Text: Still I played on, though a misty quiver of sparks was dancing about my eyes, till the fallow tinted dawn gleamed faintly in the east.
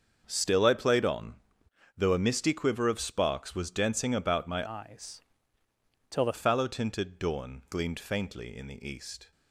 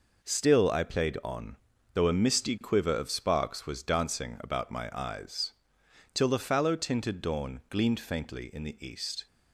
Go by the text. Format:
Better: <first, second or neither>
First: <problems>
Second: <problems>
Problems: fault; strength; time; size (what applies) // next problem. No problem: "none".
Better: second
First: starts louder than the rest; until 1.2 s; 7 dB // changes voice from "eyes" to "the"; from 4.6 to 6.3 s; 1.7 s long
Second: none